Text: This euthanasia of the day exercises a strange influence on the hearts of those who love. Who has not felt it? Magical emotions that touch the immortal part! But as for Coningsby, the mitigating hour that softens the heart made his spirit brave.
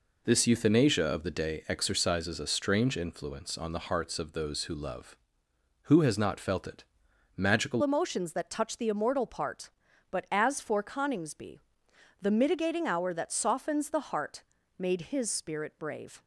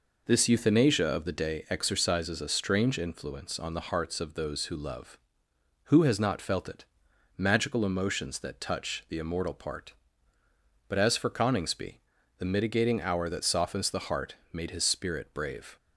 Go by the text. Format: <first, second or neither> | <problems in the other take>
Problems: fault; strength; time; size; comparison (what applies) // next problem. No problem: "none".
second | changes voice at "emotions"; from 7.8 s on; 8.4 s long // pauses between "heart" and "made"; slight; at 14.4 s; 0.36 s long; slight in the second